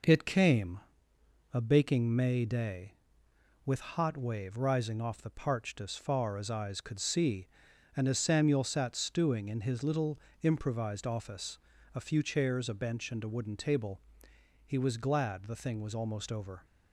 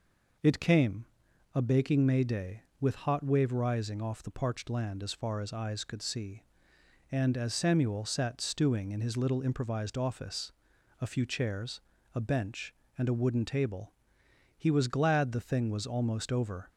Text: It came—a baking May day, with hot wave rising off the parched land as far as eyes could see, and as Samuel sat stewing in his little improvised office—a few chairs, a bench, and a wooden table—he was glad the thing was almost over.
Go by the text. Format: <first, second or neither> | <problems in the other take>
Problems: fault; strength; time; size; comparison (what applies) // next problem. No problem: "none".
second | skips "land"; at 5.8 s // pauses between "little" and "improvised"; slight; at 10.1 s; 0.24 s long